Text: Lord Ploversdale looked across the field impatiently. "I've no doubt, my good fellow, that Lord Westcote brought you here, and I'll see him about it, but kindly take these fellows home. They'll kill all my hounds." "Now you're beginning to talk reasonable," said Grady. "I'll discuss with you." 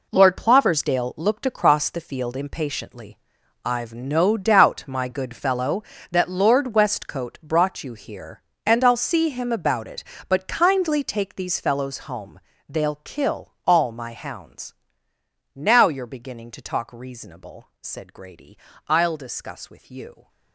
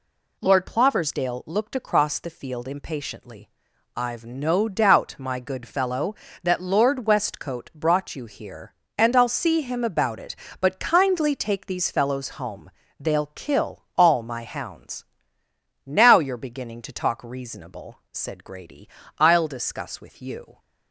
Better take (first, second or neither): second